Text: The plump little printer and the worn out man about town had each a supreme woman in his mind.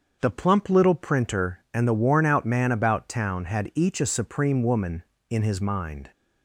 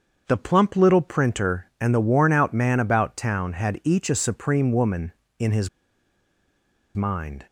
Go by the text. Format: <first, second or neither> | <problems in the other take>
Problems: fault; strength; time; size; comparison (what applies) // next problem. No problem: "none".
first | starts louder than the rest; until 1.2 s; 7 dB; also in the first // pauses between "his" and "mind"; strong; at 5.6 s; 1.2 s long